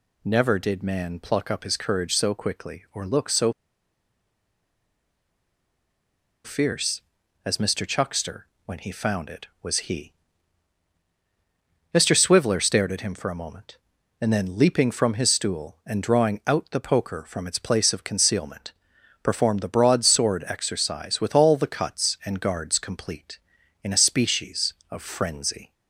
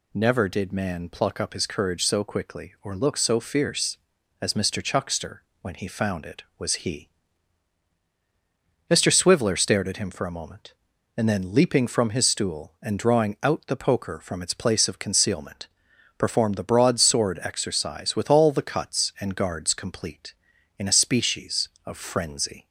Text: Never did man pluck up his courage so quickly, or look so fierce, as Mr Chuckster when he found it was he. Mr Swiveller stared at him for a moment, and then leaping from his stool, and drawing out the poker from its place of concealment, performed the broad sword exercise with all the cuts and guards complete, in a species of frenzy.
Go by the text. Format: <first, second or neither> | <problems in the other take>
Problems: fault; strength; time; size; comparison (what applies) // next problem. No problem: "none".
second | pauses between "so" and "fierce"; strong; at 3.5 s; 2.9 s long // pauses between "Chuckster" and "when"; slight; at 8.4 s; 0.18 s long; slight in the second